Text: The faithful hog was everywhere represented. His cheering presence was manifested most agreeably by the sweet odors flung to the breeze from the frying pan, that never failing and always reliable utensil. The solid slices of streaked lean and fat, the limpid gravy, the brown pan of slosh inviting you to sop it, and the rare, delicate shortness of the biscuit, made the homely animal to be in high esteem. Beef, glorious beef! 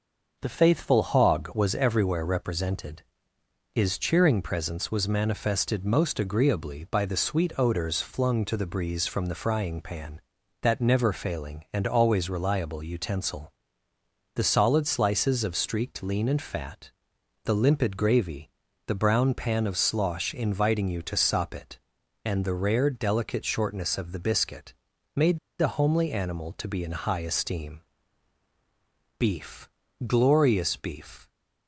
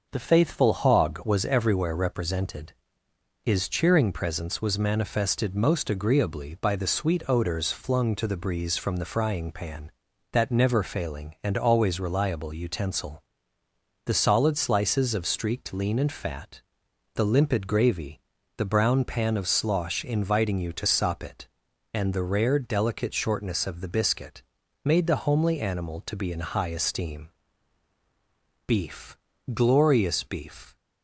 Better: second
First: pauses between "made" and "the"; slight; at 25.3 s; 0.21 s long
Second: none

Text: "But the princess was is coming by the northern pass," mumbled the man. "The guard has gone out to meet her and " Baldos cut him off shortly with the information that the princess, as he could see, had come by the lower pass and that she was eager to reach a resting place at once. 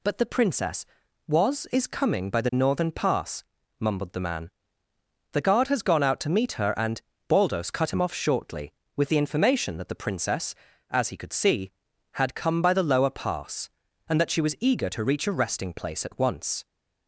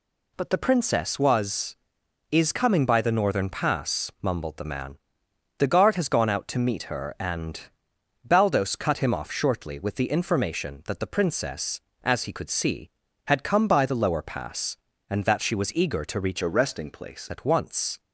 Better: first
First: none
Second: changes voice from "a" to "place"; from 16.4 to 17.2 s; 0.8 s long

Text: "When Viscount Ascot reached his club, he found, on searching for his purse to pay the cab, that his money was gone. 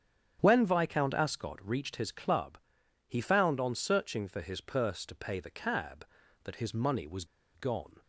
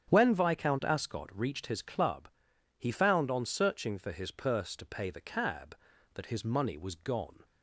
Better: second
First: starts louder than the rest; strong; until 1.4 s; 9 dB // pauses between "was" and "gone"; slight; at 7.2 s; 0.30 s long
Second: starts louder than the rest; strong; until 1.1 s; 9 dB

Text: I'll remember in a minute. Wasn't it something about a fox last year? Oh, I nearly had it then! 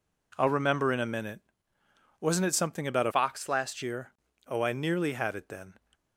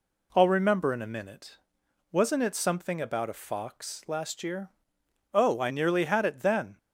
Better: second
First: changes voice from "fox" to "last"; from 3.1 to 3.8 s; 0.7 s long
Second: none

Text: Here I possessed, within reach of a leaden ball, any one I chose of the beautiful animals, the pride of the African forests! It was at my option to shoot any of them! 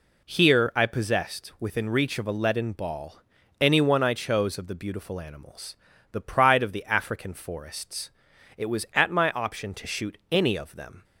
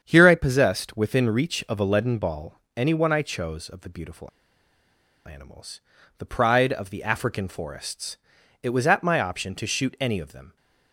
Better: first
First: none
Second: starts louder than the rest; strong; until 1.0 s; 8 dB // pauses between "beautiful" and "animals"; at 4.2 s; 0.98 s long

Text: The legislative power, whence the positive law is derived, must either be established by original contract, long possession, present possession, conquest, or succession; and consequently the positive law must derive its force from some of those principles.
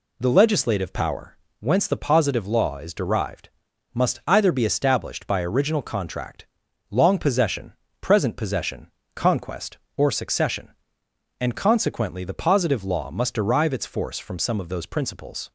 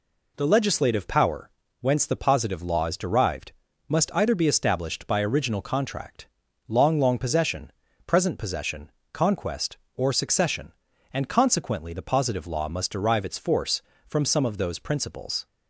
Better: first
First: none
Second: says "long" twice; at 6.9 s

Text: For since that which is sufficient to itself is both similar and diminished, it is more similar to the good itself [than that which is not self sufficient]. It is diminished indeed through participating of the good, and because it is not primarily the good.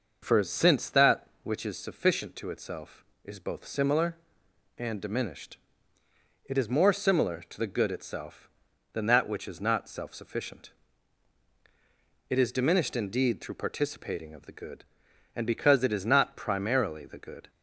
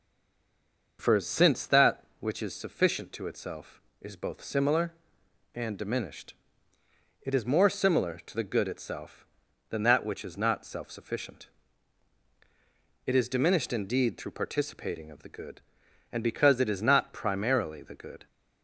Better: first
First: none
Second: stays silent before the first word; until 0.9 s; 0.9 s long

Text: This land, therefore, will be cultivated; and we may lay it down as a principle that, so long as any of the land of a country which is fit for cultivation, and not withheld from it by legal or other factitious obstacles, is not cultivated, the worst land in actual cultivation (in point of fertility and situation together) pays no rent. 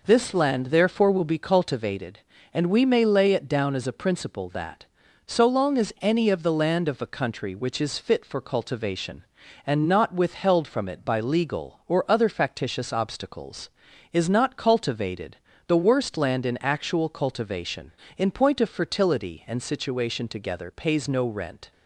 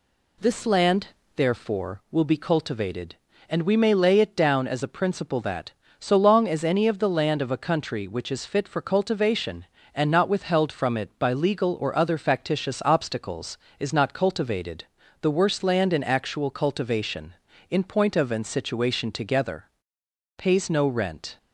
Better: first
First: none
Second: skips "fertility"; at 18.3 s

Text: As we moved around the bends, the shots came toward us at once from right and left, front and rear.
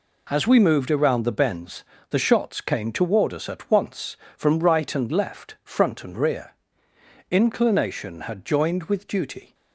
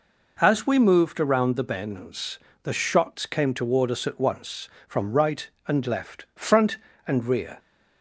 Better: second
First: goes on to say "Inclination had joined with duty"; strong; from 7.2 s on; 2.2 s long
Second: none

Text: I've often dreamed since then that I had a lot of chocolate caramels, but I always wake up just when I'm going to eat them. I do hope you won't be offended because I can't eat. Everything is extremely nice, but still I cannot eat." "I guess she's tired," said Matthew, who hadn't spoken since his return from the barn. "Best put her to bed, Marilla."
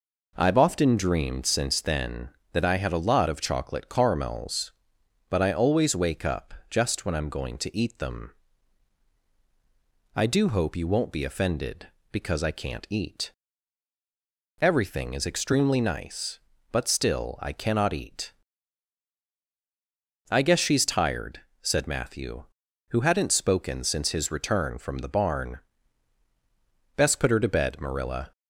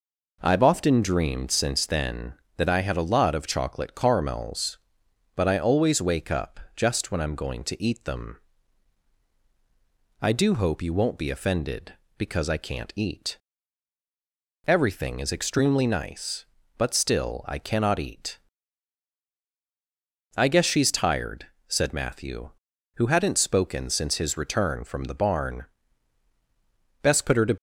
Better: first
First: pauses between "up" and "just"; slight; at 6.5 s; 0.16 s long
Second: pauses between "up" and "just"; slight; at 6.5 s; 0.16 s long // stops before "bed Marilla"; at 27.5 s

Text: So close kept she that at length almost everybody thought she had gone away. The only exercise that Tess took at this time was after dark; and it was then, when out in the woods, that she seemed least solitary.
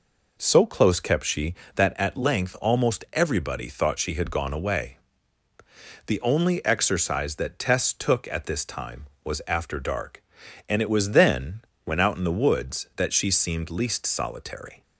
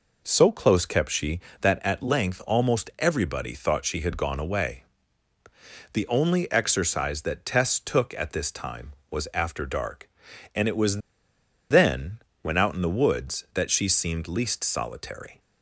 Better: first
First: none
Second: pauses between "was" and "then"; noticeable; at 10.9 s; 0.70 s long

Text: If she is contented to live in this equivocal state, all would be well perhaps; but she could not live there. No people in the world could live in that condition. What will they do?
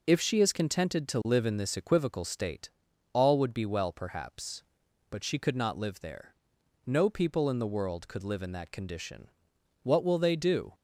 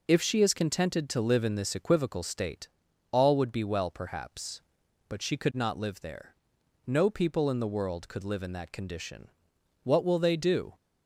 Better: neither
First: none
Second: none

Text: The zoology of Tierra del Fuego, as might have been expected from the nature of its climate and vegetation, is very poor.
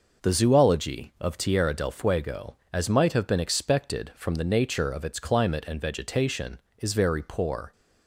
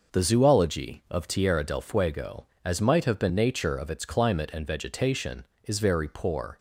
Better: first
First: none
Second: skips "expected from the"; at 3.2 s

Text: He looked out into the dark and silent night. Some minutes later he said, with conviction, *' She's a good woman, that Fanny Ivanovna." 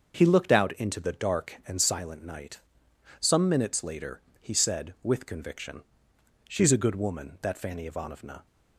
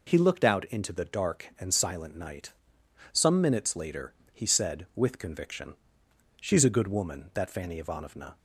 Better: second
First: starts louder than the rest; until 1.9 s; 7 dB // pauses between "later" and "he"; slight; at 4.2 s; 0.18 s long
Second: pauses between "later" and "he"; slight; at 4.1 s; 0.18 s long

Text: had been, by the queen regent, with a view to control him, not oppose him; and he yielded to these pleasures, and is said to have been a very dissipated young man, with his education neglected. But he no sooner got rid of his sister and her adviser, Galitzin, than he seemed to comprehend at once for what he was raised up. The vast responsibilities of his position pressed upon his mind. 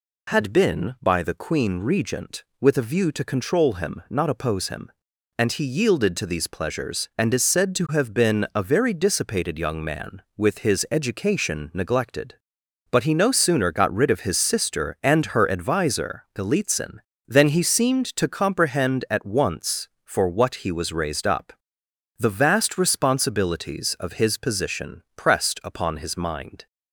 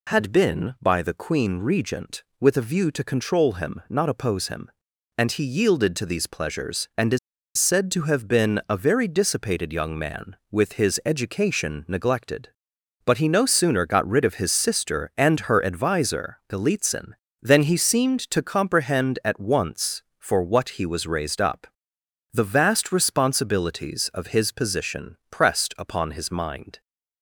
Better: first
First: none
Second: pauses between "is" and "said"; at 7.1 s; 0.39 s long

